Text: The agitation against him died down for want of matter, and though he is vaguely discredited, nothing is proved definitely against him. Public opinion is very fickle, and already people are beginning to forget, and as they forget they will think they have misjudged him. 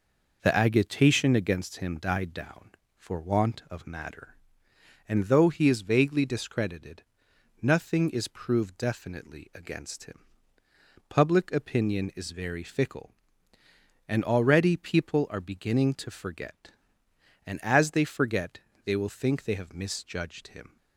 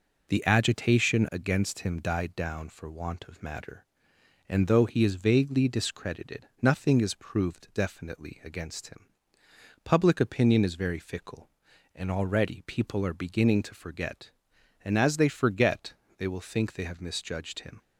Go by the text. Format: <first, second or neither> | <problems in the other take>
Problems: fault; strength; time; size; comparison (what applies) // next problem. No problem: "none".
neither | pauses between "forget" and "they"; slight; the same in both